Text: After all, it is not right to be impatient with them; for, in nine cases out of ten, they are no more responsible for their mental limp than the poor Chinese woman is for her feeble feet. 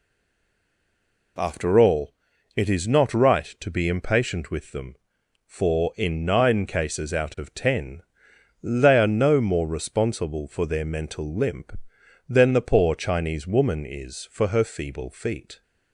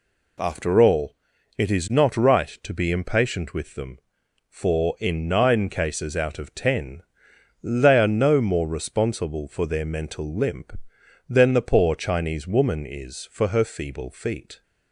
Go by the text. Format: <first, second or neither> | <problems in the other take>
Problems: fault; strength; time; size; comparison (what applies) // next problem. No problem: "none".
second | stays silent before the first word; noticeable; until 1.3 s; 1.3 s long